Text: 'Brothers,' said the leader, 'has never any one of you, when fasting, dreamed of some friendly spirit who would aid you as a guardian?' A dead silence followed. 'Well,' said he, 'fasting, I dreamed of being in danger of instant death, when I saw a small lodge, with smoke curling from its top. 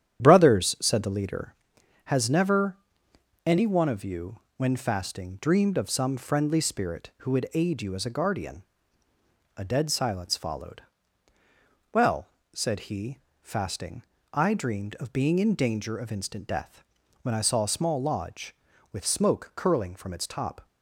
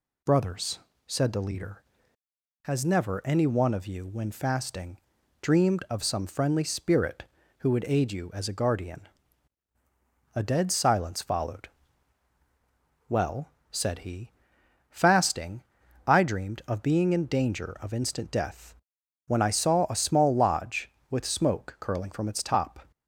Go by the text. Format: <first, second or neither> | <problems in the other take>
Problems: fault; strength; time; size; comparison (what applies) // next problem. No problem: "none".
second | starts louder than the rest; strong; until 1.5 s; 10 dB // pauses between "never" and "any"; noticeable; at 2.7 s; 0.70 s long